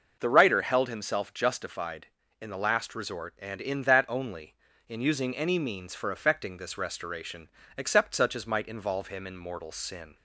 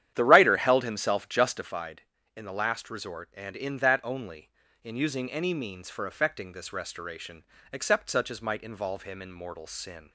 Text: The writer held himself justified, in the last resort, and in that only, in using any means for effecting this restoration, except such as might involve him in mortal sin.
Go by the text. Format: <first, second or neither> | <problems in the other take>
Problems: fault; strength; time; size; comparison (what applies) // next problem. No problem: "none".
first | starts louder than the rest; strong; until 1.9 s; 10.5 dB